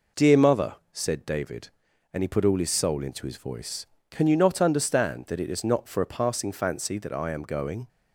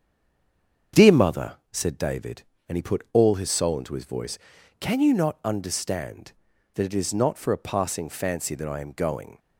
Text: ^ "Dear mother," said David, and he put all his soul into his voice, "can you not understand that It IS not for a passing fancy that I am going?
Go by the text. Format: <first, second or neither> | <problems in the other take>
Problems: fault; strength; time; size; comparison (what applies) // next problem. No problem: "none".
first | stays silent before the first word; slight; until 0.9 s; 0.9 s long // starts louder than the rest; strong; until 2.1 s; 7 dB